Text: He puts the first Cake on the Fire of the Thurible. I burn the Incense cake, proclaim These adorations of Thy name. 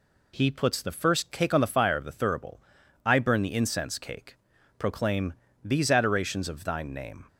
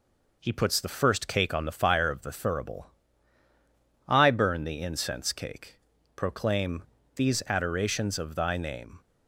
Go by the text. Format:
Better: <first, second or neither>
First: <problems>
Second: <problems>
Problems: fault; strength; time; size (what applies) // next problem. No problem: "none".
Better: second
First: pauses between "proclaim" and "These"; slight; at 5.3 s; 0.30 s long // says "Thine" for "Thy"; at 6.6 s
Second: pauses between "proclaim" and "These"; slight; at 6.8 s; 0.32 s long